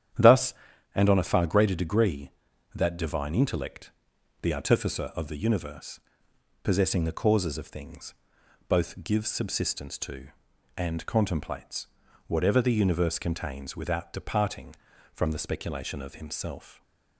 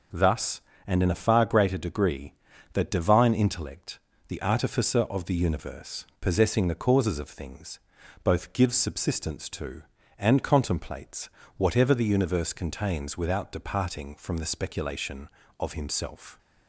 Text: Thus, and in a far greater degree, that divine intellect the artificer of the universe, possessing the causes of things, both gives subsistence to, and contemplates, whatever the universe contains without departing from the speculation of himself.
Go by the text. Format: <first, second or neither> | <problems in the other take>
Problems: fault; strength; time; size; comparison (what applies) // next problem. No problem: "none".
second | starts louder than the rest; strong; until 1.6 s; 10 dB // says "on" for "in"; at 1.0 s // pauses between "intellect" and "the"; noticeable; at 3.9 s; 0.50 s long; slight in the second